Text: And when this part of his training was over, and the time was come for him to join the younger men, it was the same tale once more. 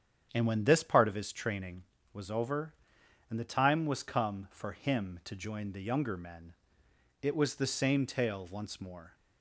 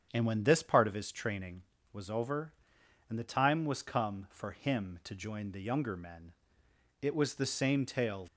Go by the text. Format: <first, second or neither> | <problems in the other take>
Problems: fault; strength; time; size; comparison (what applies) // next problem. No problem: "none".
first | starts louder than the rest; strong; until 1.1 s; 8 dB; strong in the first // stops before "once more"; at 8.2 s